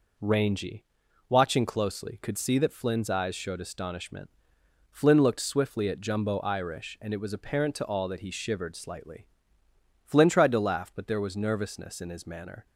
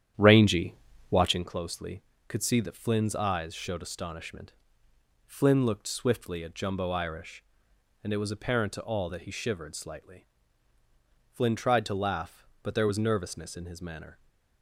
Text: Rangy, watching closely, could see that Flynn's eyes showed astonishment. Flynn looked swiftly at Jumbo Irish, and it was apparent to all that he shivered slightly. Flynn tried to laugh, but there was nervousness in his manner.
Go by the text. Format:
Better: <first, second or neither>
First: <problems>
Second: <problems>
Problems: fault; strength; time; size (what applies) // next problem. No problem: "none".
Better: first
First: none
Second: starts louder than the rest; strong; until 1.4 s; 10 dB